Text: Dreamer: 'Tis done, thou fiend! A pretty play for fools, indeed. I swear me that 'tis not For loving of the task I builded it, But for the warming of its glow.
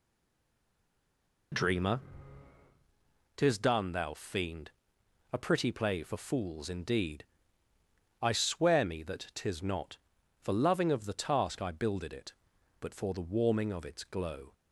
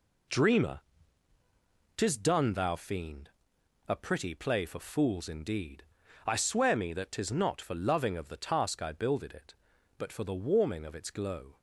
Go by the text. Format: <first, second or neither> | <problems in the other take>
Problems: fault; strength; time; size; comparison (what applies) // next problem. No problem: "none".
second | stays silent before the first word; noticeable; until 1.5 s; 1.5 s long